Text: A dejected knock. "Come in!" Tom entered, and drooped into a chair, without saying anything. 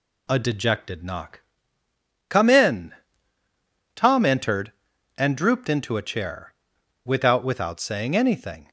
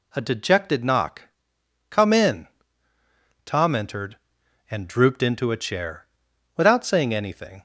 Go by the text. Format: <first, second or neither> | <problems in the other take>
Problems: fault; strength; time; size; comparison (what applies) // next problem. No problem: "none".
second | says "without" twice; at 7.4 s